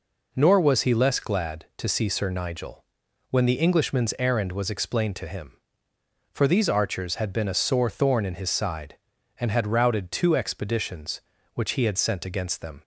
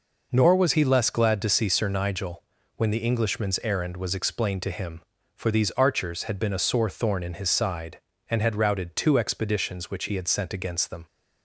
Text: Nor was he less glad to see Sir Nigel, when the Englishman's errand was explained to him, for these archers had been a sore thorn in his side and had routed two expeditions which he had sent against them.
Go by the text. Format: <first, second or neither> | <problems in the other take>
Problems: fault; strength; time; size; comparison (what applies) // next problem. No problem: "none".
neither | none